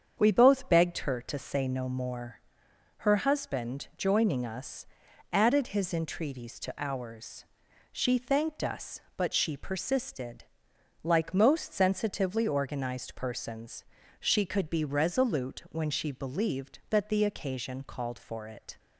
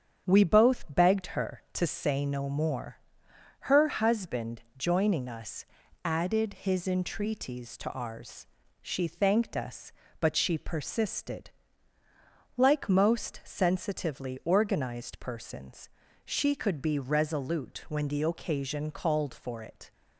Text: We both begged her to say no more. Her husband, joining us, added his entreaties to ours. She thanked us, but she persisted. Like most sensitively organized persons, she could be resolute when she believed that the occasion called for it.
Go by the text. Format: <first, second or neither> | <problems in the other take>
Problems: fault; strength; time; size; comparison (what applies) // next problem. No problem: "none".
first | starts louder than the rest; strong; until 1.3 s; 8 dB; strong in the first // skips "she believed that"; at 18.0 s